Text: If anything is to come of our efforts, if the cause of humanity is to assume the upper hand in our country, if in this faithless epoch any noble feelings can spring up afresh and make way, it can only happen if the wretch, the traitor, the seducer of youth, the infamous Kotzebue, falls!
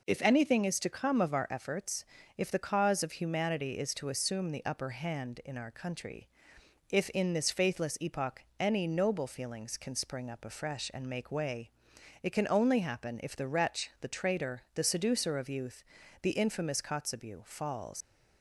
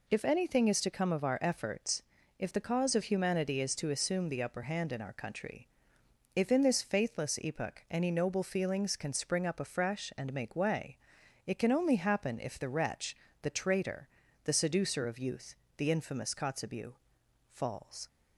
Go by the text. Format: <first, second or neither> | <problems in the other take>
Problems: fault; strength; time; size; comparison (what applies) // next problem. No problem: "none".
second | pauses between "epoch" and "any"; slight; at 8.4 s; 0.18 s long // leaves "falls" unfinished; at 18.0 s; 115 ms